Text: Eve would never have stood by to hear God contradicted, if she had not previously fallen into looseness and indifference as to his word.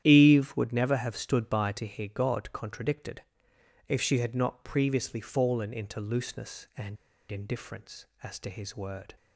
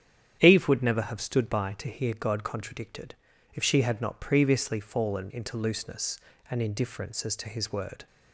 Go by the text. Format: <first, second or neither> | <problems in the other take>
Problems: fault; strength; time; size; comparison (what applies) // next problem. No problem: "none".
second | starts louder than the rest; strong; until 1.0 s; 10.5 dB; strong in the second // pauses between "and" and "indifference"; slight; at 6.9 s; 0.34 s long